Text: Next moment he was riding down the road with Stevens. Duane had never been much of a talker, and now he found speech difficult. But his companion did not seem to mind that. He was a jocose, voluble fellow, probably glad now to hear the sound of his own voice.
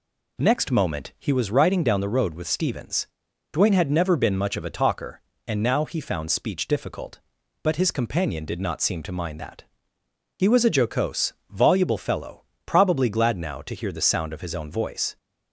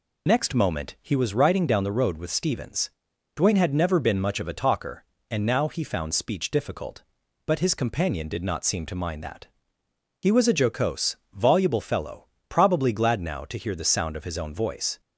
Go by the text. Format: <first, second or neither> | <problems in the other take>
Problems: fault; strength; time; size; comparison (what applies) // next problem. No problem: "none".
first | loses the start of "Next"; at 0.2 s; 40 ms